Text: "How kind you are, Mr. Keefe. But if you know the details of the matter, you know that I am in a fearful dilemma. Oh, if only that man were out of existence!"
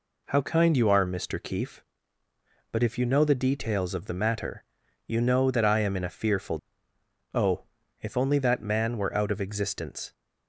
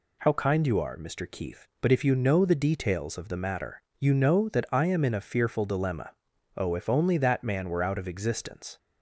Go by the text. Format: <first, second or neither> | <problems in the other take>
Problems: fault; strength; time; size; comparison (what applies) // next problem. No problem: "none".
second | skips "dilemma"; at 6.9 s